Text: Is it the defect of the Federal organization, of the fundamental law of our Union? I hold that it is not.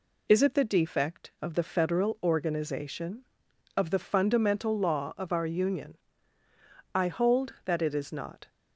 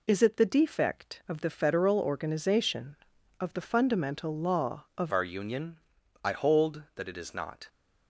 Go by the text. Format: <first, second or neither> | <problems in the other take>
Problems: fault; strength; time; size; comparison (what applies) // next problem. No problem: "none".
first | changes voice at "our"; from 5.1 s on; 2.5 s long